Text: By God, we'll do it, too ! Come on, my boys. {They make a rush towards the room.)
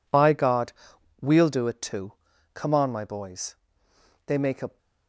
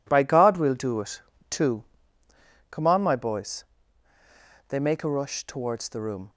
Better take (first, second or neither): second